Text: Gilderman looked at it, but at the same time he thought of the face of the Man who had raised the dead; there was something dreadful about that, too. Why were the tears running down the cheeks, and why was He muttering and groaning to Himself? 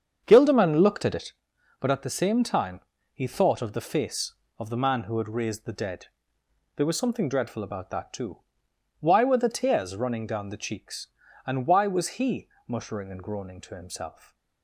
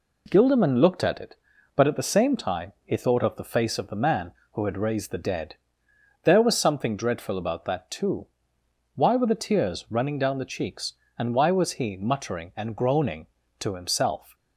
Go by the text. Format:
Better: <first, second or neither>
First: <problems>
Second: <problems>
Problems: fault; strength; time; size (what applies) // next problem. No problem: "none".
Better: second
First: starts louder than the rest; strong; until 1.3 s; 7 dB // pauses between "time" and "he"; slight; at 2.7 s; 0.32 s long // pauses between "He" and "muttering"; slight; at 12.4 s; 0.20 s long // stays silent after the last word; slight; from 14.1 s on; 0.5 s long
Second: none